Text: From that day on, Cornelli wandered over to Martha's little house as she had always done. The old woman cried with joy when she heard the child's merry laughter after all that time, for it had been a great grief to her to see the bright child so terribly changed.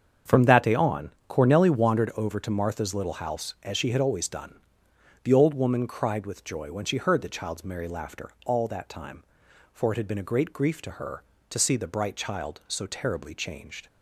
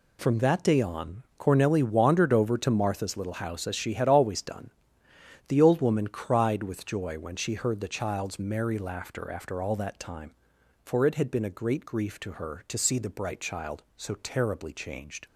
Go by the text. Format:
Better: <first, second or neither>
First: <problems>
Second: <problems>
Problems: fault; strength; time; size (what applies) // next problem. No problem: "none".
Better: second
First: starts louder than the rest; strong; until 1.4 s; 7.5 dB // skips "after"; at 8.3 s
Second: none